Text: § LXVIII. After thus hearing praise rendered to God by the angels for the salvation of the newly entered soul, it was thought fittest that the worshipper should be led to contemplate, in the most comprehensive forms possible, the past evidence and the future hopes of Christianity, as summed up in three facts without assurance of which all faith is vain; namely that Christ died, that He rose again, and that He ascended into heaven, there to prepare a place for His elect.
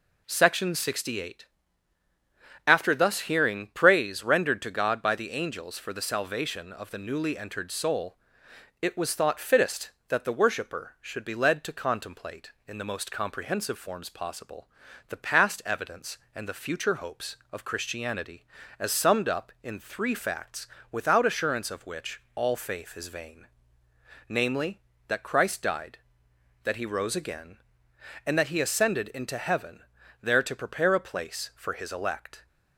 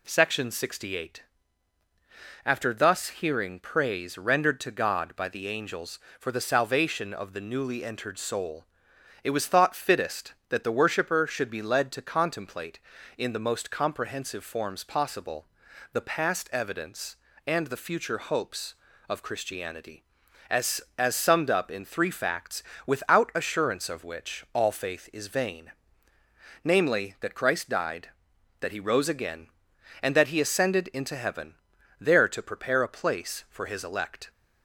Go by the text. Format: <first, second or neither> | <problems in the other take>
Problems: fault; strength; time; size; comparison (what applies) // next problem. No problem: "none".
first | says "as" twice; at 20.9 s // pauses between "facts" and "without"; slight; at 22.6 s; 0.24 s long; slight in the first